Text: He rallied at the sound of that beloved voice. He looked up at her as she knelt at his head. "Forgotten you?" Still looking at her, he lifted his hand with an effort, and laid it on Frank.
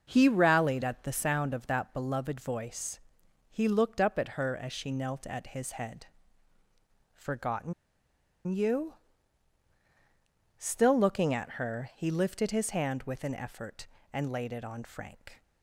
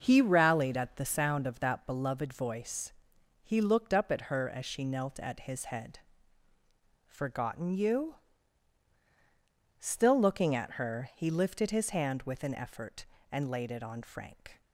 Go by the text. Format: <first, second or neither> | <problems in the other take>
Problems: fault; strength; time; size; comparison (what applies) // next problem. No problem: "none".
second | starts louder than the rest; noticeable; until 1.1 s; 6 dB; noticeable in the second // pauses between "Forgotten" and "you"; noticeable; at 7.7 s; 0.74 s long